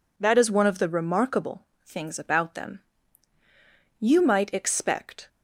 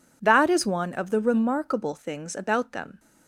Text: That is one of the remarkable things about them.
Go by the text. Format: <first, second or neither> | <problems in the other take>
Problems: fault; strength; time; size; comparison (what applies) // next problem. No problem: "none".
second | pauses between "remarkable" and "things"; slight; at 1.6 s; 0.22 s long // goes on to say "You might expect"; noticeable; from 3.9 s on; 1.2 s long